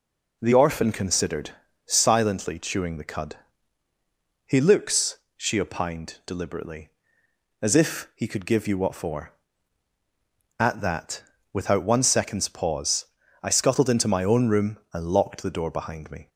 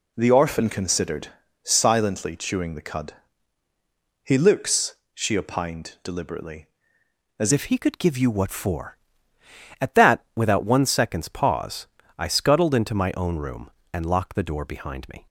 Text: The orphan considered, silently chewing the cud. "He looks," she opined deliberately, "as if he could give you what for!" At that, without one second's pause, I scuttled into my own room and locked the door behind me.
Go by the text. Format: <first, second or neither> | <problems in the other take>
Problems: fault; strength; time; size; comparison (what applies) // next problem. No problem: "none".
first | changes voice at "if"; from 7.5 s on; 7.7 s long